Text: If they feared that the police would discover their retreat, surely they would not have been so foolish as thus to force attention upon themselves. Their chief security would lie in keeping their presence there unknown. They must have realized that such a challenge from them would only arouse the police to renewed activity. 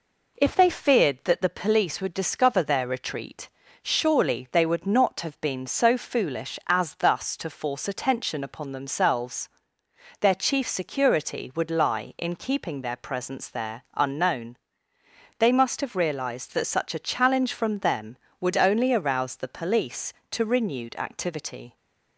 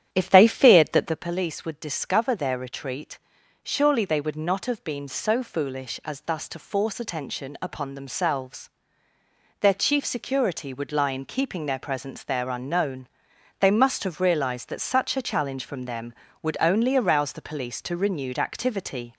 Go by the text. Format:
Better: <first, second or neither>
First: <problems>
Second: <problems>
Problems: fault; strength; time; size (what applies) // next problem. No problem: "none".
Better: first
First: none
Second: starts louder than the rest; strong; until 1.2 s; 10 dB